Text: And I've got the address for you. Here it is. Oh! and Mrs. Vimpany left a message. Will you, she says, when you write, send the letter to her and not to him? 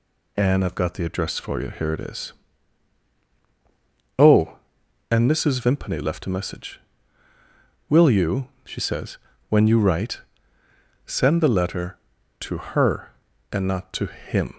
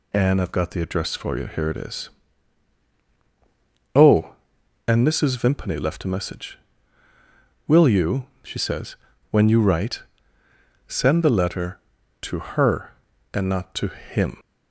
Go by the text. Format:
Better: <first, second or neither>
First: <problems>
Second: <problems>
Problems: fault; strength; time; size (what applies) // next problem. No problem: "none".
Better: neither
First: none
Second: none